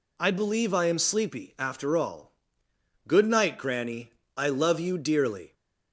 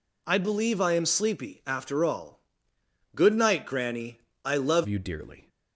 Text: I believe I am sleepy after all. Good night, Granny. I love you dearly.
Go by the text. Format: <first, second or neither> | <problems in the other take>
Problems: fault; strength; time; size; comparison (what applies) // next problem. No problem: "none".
first | changes voice at "you"; from 4.8 s on; 0.6 s long